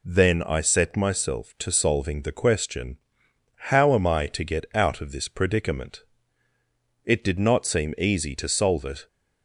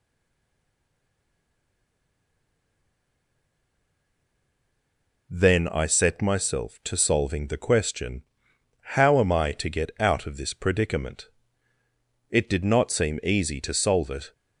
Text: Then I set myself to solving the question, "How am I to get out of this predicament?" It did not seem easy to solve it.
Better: first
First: none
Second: stays silent before the first word; strong; until 5.3 s; 5.3 s long

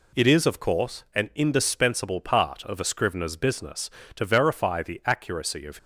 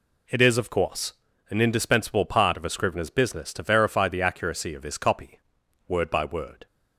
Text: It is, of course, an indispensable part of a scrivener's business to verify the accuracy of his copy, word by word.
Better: second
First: stops before "his copy word by word"; at 5.7 s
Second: none

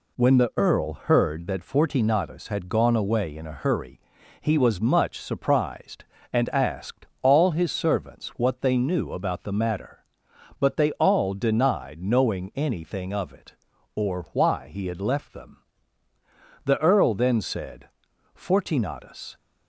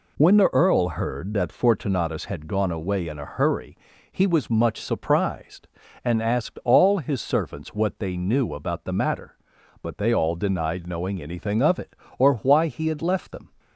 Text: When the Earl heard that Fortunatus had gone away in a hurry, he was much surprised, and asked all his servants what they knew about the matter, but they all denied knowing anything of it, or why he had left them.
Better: second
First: pauses between "asked" and "all"; slight; at 7.0 s; 0.16 s long // goes on to say "The Earl then said Fortunatus"; strong; from 16.6 s on; 2.7 s long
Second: none

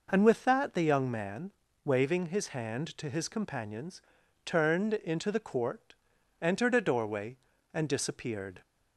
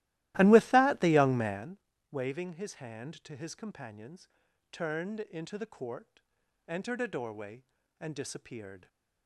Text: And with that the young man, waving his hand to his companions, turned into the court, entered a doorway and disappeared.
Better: first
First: none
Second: starts louder than the rest; strong; until 1.8 s; 16 dB

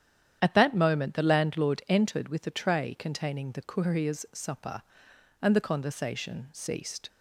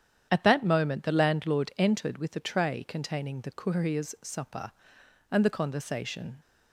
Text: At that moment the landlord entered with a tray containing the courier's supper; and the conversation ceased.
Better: first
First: starts louder than the rest; strong; until 1.4 s; 9.5 dB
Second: starts louder than the rest; strong; until 1.3 s; 9 dB // stops before "ceased"; at 6.4 s

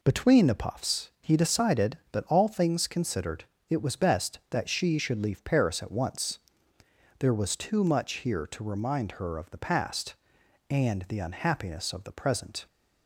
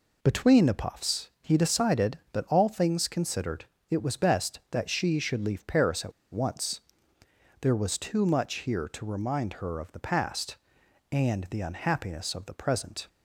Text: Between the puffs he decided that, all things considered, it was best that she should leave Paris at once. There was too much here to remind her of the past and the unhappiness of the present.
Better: first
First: none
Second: pauses between "at" and "once"; slight; at 6.1 s; 0.19 s long

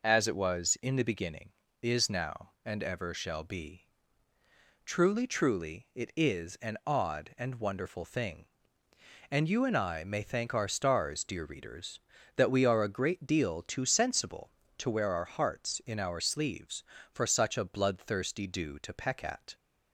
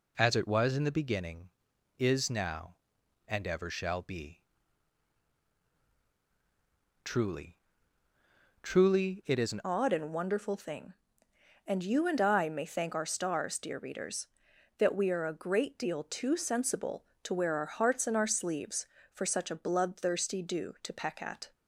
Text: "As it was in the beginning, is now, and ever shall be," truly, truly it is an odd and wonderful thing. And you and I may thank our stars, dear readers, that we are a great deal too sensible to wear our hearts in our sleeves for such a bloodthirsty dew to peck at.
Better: first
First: none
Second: changes voice at "odd"; from 9.6 s on; 11.9 s long

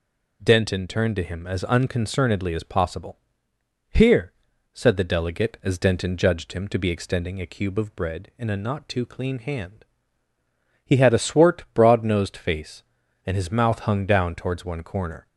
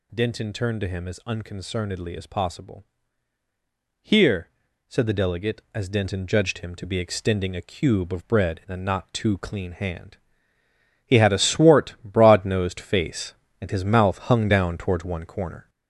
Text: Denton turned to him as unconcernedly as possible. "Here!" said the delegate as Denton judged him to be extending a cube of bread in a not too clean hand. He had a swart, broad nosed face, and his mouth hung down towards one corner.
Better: first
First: none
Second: gets louder; noticeable; throughout; 4 dB

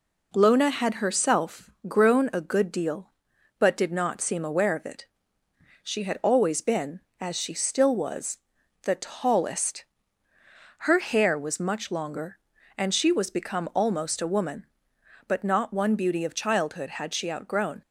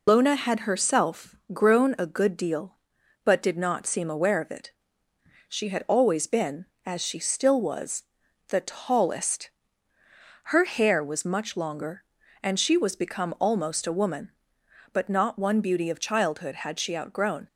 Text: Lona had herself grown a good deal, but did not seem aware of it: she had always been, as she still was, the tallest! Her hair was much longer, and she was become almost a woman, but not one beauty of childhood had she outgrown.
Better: first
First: pauses between "herself" and "grown"; slight; at 1.6 s; 0.20 s long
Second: loses the start of "Lona"; at 0.0 s; 90 ms // pauses between "herself" and "grown"; slight; at 1.3 s; 0.20 s long

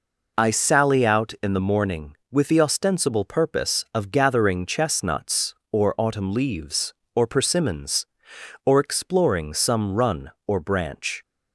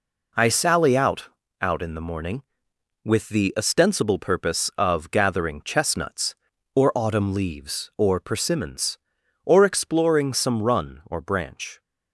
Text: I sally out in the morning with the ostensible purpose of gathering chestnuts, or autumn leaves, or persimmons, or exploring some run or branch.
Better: first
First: none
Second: says "out" twice; at 1.6 s

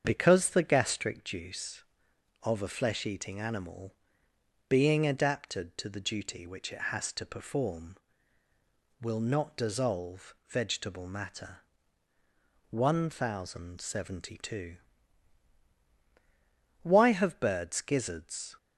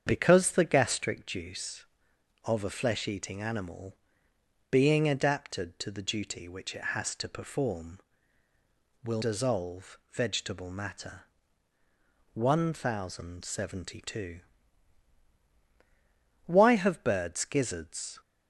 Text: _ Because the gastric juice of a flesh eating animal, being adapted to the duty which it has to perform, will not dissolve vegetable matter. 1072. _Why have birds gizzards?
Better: first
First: starts louder than the rest; strong; until 1.0 s; 7.5 dB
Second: starts louder than the rest; strong; until 1.0 s; 7.5 dB // skips "not"; at 9.2 s

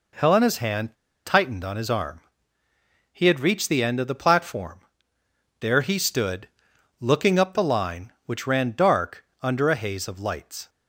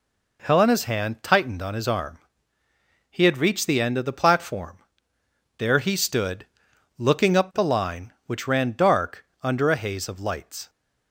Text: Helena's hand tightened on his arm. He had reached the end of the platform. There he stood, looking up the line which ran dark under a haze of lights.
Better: second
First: pauses between "hand" and "tightened"; slight; at 0.9 s; 0.29 s long // pauses between "dark" and "under"; slight; at 9.2 s; 0.16 s long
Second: pauses between "dark" and "under"; slight; at 9.2 s; 0.16 s long

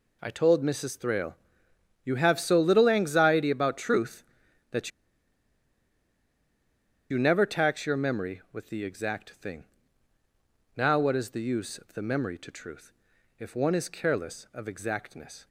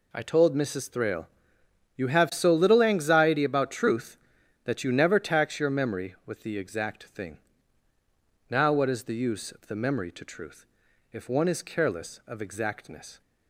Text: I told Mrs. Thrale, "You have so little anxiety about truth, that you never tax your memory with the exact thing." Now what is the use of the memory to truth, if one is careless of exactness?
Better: second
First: pauses between "that" and "you"; strong; at 4.9 s; 2.2 s long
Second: none

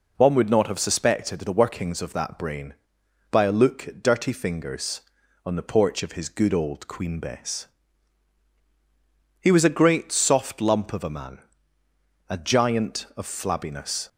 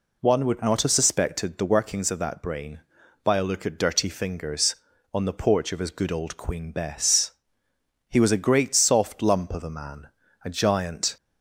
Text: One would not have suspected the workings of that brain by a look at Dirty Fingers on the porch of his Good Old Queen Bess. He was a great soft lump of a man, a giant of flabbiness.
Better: first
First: none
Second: stops before "of flabbiness"; at 11.1 s

